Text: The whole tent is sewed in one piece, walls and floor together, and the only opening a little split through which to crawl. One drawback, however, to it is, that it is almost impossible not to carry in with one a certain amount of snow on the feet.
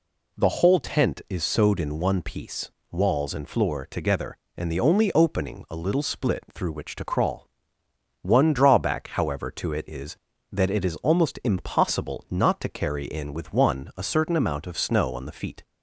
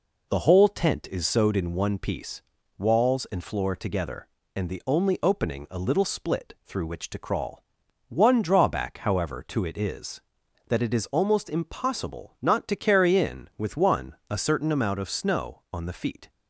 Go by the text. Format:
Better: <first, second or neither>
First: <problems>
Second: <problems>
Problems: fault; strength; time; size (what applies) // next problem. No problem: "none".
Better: neither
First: none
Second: none